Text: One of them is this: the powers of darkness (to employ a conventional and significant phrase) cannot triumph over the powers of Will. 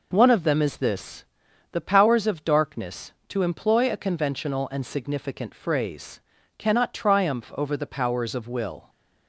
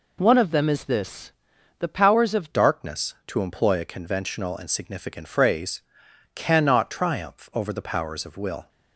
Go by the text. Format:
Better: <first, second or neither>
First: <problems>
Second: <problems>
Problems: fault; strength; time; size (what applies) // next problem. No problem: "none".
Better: first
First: none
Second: changes voice at "darkness"; from 2.5 s on; 6.1 s long